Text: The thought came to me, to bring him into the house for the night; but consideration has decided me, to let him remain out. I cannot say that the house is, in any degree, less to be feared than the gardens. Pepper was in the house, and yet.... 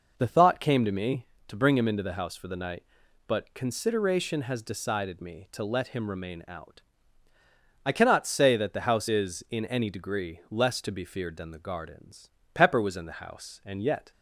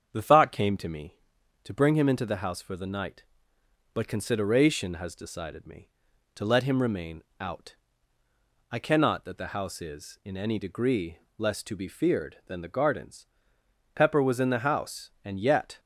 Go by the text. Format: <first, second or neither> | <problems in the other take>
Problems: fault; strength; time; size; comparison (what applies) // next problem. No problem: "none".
first | starts louder than the rest; strong; until 1.1 s; 7.5 dB // pauses between "remain" and "out"; slight; at 7.2 s; 0.18 s long // skips "say"; at 9.2 s